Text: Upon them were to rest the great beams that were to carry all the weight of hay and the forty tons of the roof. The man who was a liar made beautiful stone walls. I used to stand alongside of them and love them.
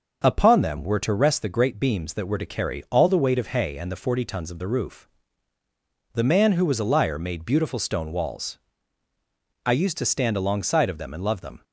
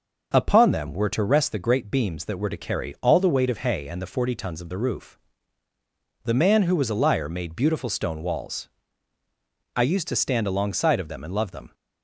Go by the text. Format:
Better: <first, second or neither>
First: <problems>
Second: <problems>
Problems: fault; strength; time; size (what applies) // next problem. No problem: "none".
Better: neither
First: starts louder than the rest; noticeable; until 1.2 s; 6 dB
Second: starts louder than the rest; noticeable; until 1.3 s; 6 dB